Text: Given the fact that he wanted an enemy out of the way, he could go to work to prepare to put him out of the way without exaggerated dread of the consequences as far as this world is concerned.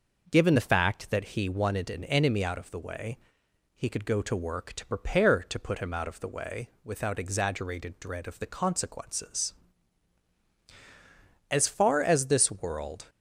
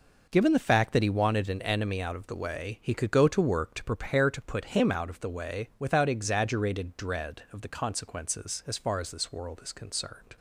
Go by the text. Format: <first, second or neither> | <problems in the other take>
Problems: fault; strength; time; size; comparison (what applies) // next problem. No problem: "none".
second | pauses between "way" and "without"; slight; at 6.6 s; 0.16 s long // stops before "is concerned"; at 13.0 s